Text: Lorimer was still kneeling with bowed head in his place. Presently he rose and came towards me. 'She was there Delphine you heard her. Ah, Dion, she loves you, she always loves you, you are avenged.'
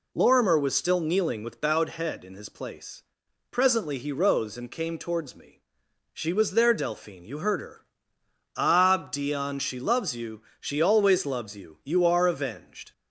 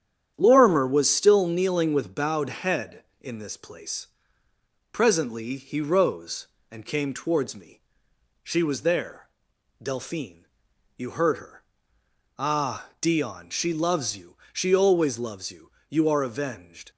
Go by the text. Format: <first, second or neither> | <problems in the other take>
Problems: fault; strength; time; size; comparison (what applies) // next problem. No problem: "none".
first | starts louder than the rest; strong; until 1.3 s; 9.5 dB // says "this" for "his"; at 3.3 s // pauses between "there" and "Delphine"; noticeable; at 9.2 s; 0.52 s long // pauses between "Delphine" and "you"; noticeable; at 10.4 s; 0.50 s long